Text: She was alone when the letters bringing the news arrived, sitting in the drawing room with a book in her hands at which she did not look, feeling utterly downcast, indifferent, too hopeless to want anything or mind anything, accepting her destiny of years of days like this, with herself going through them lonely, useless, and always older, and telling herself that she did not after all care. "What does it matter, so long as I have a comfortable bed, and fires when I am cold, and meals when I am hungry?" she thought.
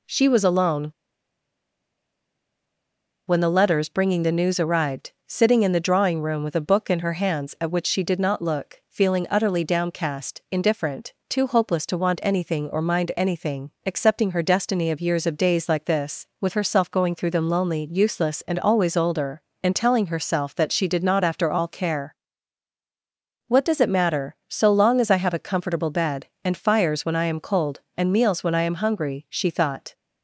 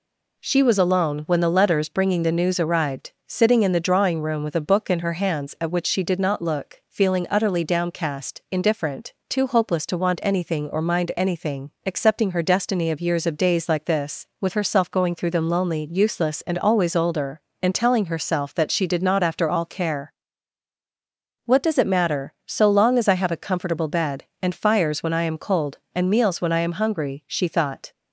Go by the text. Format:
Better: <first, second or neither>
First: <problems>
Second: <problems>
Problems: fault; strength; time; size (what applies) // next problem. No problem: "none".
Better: second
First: pauses between "alone" and "when"; strong; at 0.8 s; 2.3 s long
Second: none